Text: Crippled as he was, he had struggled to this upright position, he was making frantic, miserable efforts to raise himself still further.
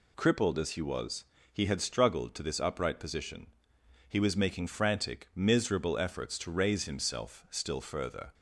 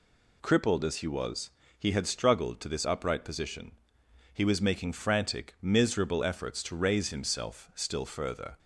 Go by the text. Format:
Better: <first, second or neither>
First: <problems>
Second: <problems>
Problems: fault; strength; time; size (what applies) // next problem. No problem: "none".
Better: neither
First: none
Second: none